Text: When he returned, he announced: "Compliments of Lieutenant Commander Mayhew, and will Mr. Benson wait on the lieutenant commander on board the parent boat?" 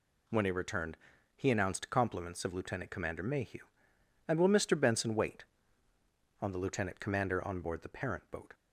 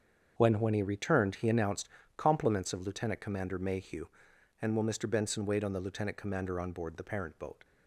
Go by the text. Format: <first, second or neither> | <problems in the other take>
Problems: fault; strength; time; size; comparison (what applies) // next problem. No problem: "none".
first | starts louder than the rest; strong; until 1.3 s; 7 dB // says "When" twice; at 0.6 s